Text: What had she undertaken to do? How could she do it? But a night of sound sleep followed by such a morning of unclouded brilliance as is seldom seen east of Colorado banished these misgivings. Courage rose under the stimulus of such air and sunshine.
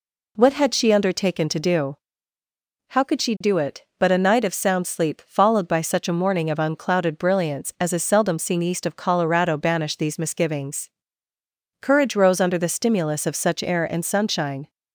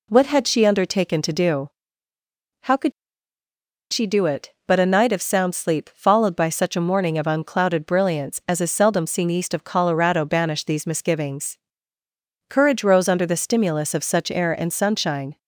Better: first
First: none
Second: pauses between "could" and "she"; at 2.9 s; 1.0 s long

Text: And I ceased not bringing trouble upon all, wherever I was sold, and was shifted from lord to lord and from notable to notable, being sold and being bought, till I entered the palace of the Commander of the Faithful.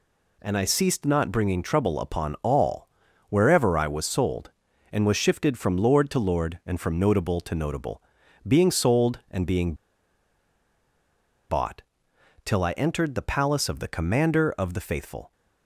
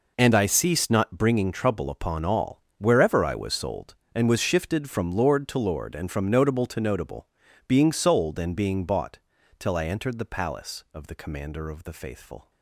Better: second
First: pauses between "being" and "bought"; strong; at 9.7 s; 1.7 s long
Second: none

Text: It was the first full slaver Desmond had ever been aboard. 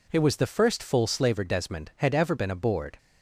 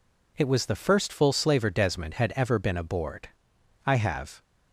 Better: first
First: none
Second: goes on to say "I have"; from 3.8 s on; 0.56 s long

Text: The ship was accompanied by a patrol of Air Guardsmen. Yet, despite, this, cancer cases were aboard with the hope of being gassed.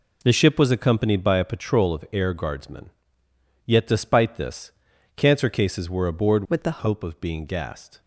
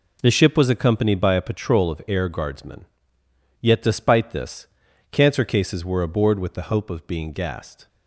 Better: second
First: changes voice from "with" to "the"; from 6.4 to 6.7 s; 0.3 s long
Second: none

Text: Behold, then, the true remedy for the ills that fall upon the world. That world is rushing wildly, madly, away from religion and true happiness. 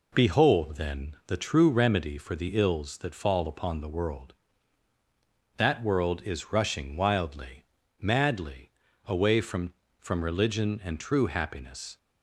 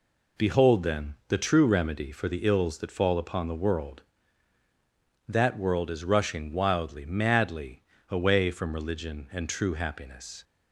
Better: second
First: says "from" twice; at 9.9 s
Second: none

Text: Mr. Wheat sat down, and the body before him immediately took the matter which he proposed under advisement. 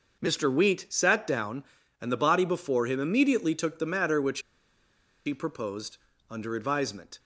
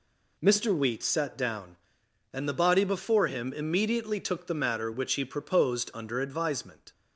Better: second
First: pauses between "which" and "he"; noticeable; at 4.4 s; 0.85 s long // pauses between "proposed" and "under"; slight; at 5.9 s; 0.34 s long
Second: none

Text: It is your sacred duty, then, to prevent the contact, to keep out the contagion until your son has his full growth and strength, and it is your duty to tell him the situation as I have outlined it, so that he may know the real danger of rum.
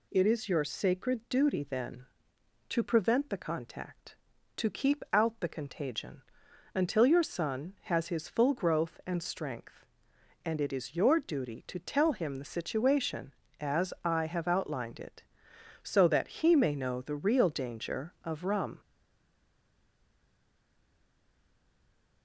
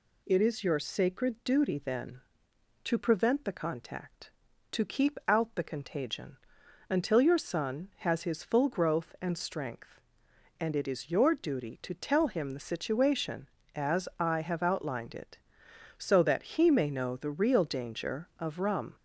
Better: second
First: pauses between "contagion" and "until"; noticeable; at 6.2 s; 0.52 s long // stays silent after the last word; strong; from 18.8 s on; 3.4 s long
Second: pauses between "contagion" and "until"; noticeable; at 6.3 s; 0.52 s long

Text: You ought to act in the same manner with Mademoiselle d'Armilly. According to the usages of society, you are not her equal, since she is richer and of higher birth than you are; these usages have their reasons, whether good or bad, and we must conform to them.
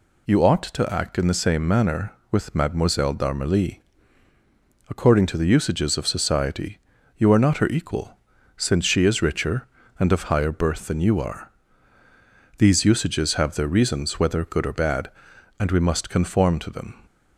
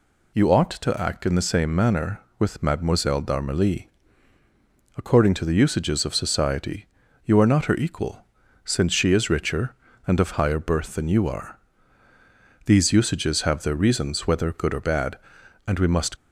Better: first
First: none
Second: stops before "conform to them"; at 16.1 s

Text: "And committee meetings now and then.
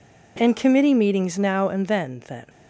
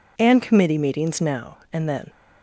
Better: second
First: says "then" twice; at 2.2 s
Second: none

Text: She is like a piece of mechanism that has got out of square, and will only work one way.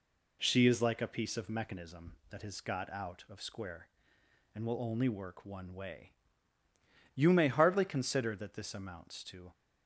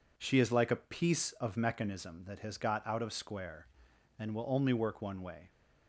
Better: second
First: goes on to say "You may hardly consider that this amounts to"; strong; from 7.1 s on; 2.3 s long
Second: none

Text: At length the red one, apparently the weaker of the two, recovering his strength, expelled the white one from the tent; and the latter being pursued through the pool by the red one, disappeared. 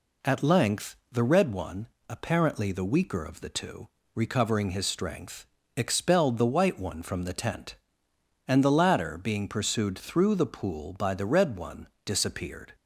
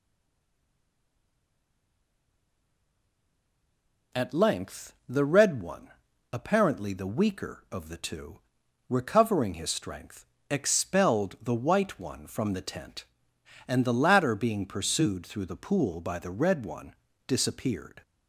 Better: first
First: none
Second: stays silent before the first word; strong; until 4.1 s; 4.1 s long

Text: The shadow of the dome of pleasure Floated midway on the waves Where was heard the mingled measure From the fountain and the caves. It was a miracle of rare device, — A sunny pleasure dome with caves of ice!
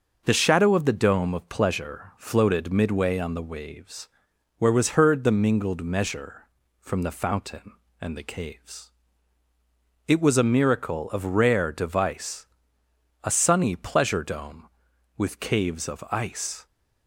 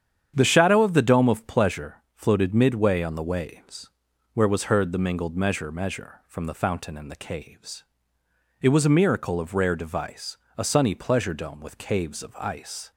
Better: first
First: starts louder than the rest; noticeable; until 1.2 s; 6 dB // pauses between "waves" and "Where"; noticeable; at 4.0 s; 0.50 s long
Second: starts louder than the rest; strong; until 1.3 s; 8.5 dB // pauses between "waves" and "Where"; at 3.8 s; 0.44 s long // says "measure" twice; at 5.7 s

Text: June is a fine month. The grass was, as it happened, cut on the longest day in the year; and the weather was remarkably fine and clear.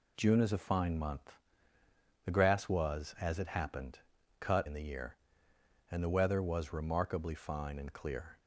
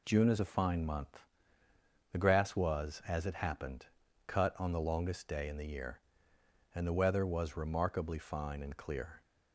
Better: second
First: skips "on the longest day"; at 4.6 s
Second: none

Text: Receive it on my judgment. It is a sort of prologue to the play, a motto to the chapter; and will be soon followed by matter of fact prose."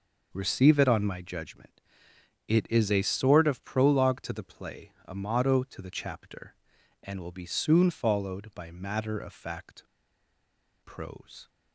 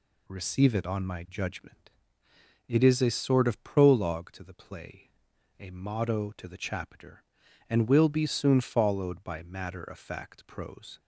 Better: second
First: pauses between "fact" and "prose"; at 9.8 s; 1.0 s long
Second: none

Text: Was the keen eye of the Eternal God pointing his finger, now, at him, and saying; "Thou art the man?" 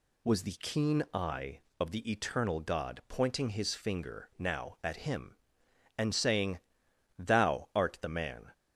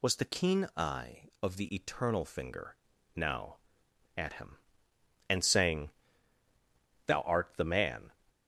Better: first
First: none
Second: skips "God pointing his"; at 2.2 s

